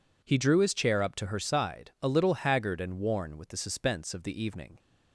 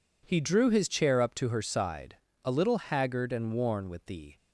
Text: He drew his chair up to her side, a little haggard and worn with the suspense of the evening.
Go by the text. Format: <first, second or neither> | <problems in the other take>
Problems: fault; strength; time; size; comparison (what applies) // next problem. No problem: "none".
first | stops before "suspense of the evening"; at 4.3 s